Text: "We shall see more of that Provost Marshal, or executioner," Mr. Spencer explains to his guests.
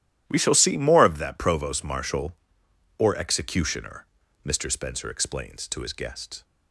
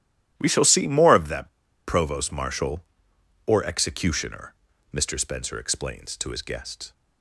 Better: first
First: starts louder than the rest; strong; until 1.2 s; 12.5 dB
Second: starts louder than the rest; strong; until 1.3 s; 12.5 dB // pauses between "that" and "Provost"; at 1.4 s; 0.36 s long

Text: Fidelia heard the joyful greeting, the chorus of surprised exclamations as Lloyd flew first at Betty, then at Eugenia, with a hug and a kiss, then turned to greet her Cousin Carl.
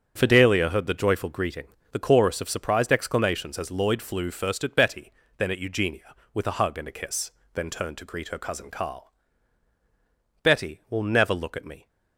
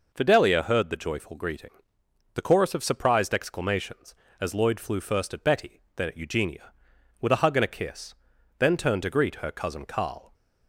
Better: second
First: starts louder than the rest; strong; until 1.1 s; 8 dB // goes on to say "Betty will never look at me"; from 10.4 s on; 1.4 s long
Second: none

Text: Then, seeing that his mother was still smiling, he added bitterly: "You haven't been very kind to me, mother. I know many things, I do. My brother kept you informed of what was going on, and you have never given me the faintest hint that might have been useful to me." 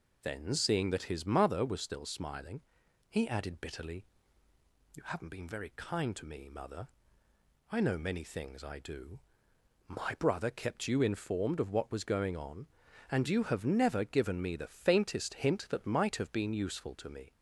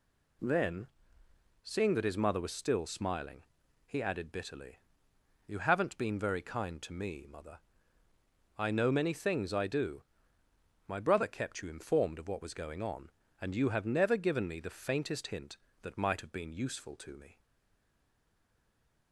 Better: first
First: none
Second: stays silent after the last word; noticeable; from 17.3 s on; 1.8 s long

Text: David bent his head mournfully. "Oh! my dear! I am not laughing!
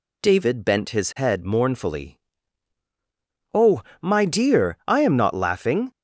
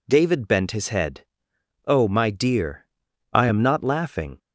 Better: first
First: none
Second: skips "mournfully"; at 1.5 s

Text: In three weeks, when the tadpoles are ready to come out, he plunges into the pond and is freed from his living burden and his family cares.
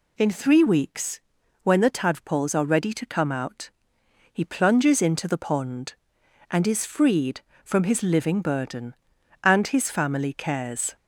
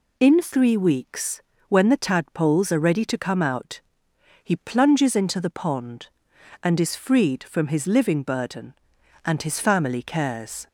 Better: neither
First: none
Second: none

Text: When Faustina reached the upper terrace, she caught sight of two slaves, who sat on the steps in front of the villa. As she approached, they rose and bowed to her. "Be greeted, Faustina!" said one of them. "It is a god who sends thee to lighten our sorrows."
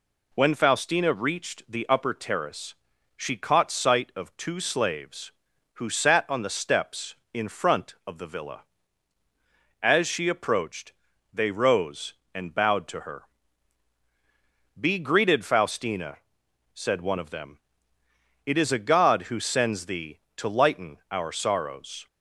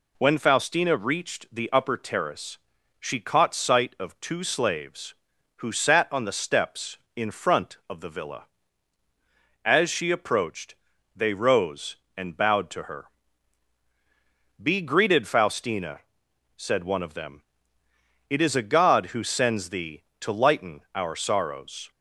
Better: neither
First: none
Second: none

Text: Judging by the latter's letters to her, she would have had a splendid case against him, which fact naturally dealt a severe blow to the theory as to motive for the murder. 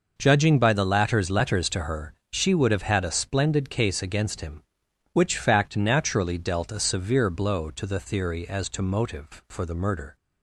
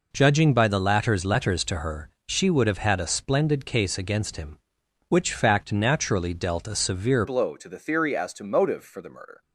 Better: first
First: none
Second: changes voice at "blow"; from 7.2 s on; 2.2 s long

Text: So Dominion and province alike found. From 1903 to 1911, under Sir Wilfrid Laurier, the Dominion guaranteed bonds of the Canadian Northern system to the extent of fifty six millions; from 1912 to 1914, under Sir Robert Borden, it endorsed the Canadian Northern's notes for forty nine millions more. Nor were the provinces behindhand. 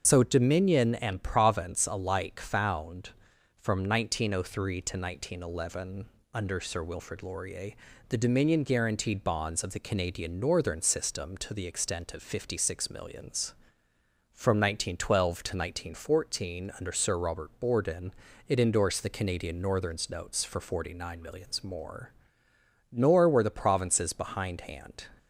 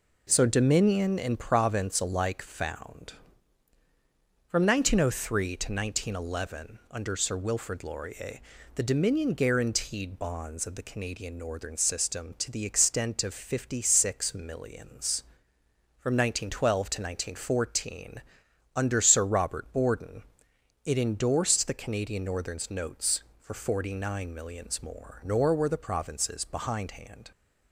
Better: second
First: loses the start of "So"; at 0.0 s; 60 ms // starts louder than the rest; until 1.0 s; 7 dB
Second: none

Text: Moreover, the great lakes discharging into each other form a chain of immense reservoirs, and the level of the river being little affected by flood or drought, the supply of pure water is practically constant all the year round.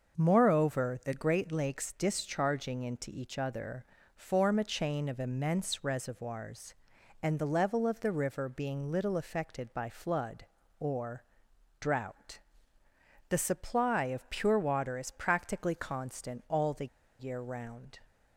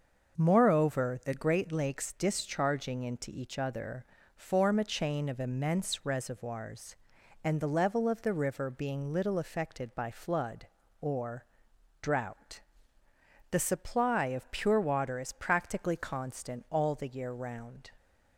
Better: second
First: starts louder than the rest; until 1.2 s; 6 dB // pauses between "other" and "form"; slight; at 3.8 s; 0.32 s long // pauses between "or" and "drought"; noticeable; at 11.2 s; 0.56 s long // pauses between "the" and "year"; slight; at 16.8 s; 0.33 s long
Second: starts louder than the rest; until 1.4 s; 6 dB // pauses between "other" and "form"; slight; at 4.0 s; 0.32 s long // pauses between "or" and "drought"; noticeable; at 11.4 s; 0.56 s long

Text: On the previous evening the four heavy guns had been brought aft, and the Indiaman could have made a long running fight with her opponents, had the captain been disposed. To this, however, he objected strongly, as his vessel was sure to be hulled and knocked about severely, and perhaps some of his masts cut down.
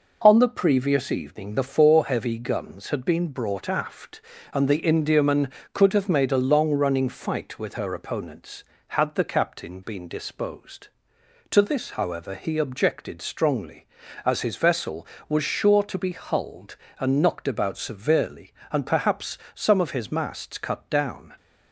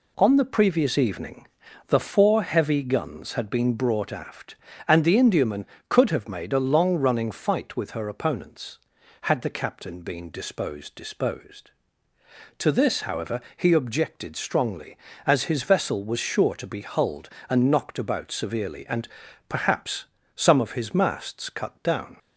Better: first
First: pauses between "perhaps" and "some"; slight; at 19.3 s; 0.16 s long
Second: pauses between "evening" and "the"; at 1.4 s; 0.44 s long // says "disposed" twice; at 10.9 s // pauses between "and" and "perhaps"; at 19.0 s; 0.42 s long // pauses between "perhaps" and "some"; slight; at 20.0 s; 0.30 s long

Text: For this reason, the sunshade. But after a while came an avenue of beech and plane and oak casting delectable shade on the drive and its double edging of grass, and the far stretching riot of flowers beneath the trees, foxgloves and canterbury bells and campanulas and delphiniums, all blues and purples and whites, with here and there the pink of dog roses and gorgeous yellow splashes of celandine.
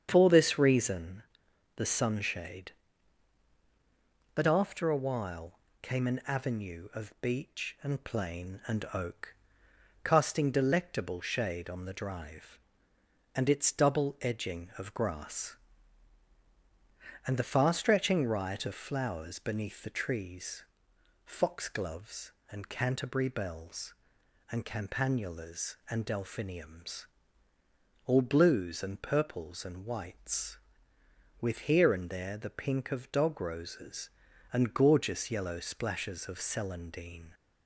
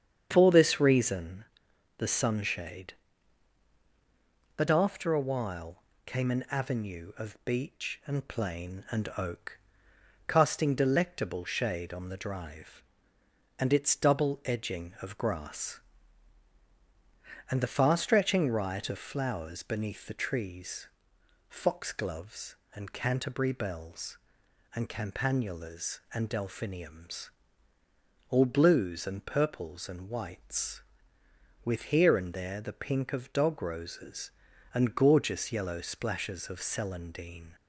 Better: neither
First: starts louder than the rest; strong; until 1.1 s; 8 dB // pauses between "while" and "came"; slight; at 5.5 s; 0.24 s long // pauses between "oak" and "casting"; noticeable; at 9.3 s; 0.72 s long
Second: starts louder than the rest; strong; until 1.3 s; 8 dB // pauses between "while" and "came"; slight; at 5.8 s; 0.24 s long // pauses between "oak" and "casting"; noticeable; at 9.5 s; 0.72 s long

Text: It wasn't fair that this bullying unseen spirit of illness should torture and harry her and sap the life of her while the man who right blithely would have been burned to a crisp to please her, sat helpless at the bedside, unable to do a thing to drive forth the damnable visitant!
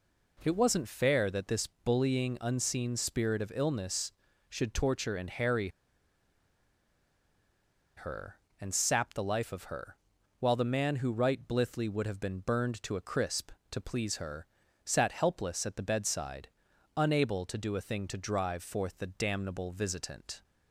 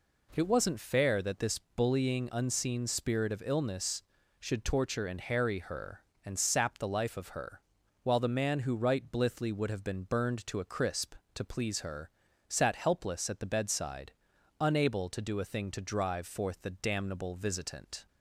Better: second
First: pauses between "harry" and "her"; strong; at 5.6 s; 2.2 s long // pauses between "her" and "while"; at 9.9 s; 0.44 s long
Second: pauses between "her" and "while"; at 7.6 s; 0.43 s long

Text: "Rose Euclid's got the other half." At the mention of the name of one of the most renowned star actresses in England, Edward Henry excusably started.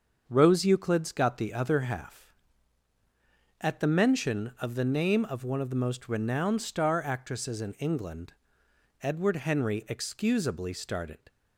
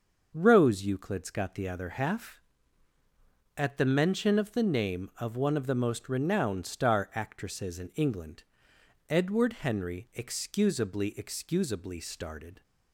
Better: first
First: starts louder than the rest; until 1.2 s; 7 dB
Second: starts louder than the rest; until 1.3 s; 6 dB // says "excusably" twice; at 11.1 s

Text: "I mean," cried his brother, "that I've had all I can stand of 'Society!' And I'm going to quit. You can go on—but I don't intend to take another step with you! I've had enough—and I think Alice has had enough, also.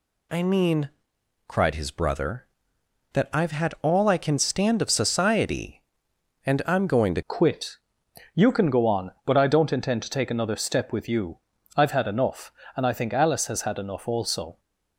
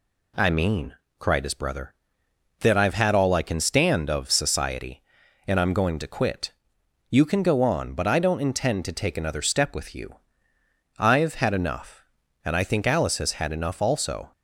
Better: second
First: changes voice at "quit"; from 7.2 s on; 7.3 s long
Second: none

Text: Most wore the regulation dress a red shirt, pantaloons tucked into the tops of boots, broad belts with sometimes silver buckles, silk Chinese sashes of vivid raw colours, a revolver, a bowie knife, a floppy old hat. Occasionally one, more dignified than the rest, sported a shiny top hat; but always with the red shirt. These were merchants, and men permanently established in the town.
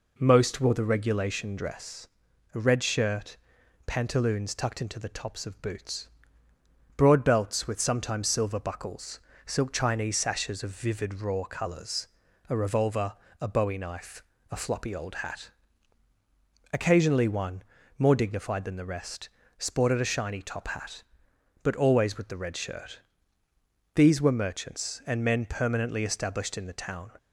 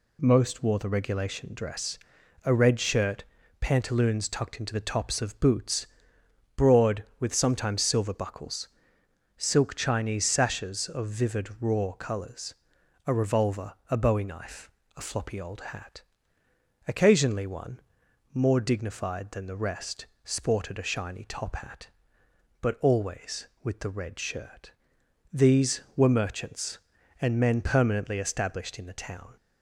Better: first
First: pauses between "dress" and "a"; noticeable; at 2.0 s; 0.46 s long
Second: pauses between "dress" and "a"; noticeable; at 1.9 s; 0.46 s long // skips "belts"; at 7.1 s

